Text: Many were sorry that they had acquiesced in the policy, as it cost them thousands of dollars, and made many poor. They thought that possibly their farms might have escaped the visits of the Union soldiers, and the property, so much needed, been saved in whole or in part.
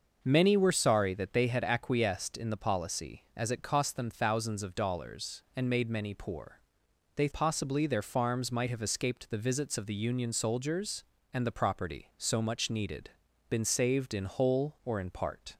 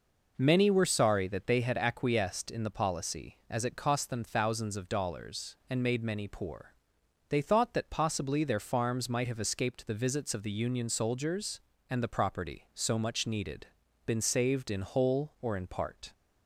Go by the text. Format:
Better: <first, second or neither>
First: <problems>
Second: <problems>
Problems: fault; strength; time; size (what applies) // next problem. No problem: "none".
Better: second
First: starts louder than the rest; noticeable; until 1.2 s; 6 dB // skips "thought that"; at 7.3 s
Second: none